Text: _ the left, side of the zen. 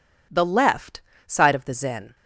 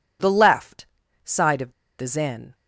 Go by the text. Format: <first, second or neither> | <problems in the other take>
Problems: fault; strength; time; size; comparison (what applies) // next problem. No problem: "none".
first | pauses between "of" and "the"; slight; at 1.7 s; 0.27 s long